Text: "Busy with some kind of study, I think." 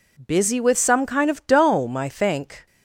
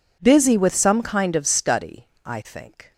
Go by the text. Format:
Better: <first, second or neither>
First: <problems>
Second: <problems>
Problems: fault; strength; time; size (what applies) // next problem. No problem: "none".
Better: second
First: says "dome" for "study"; at 1.4 s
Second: none